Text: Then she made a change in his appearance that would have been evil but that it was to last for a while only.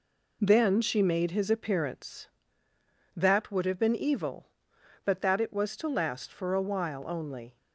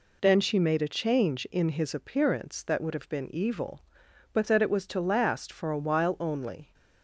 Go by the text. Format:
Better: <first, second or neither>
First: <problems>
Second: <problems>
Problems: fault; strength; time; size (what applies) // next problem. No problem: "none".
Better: second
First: skips "a change in"; at 1.3 s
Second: none